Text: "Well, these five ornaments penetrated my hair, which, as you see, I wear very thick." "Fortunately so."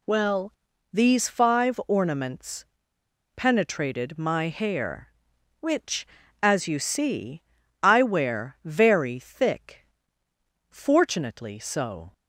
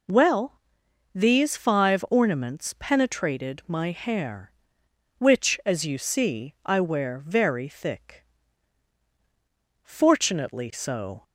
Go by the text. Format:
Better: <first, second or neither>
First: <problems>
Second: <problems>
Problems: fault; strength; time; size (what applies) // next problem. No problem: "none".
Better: second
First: pauses between "ornaments" and "penetrated"; noticeable; at 2.6 s; 0.70 s long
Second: none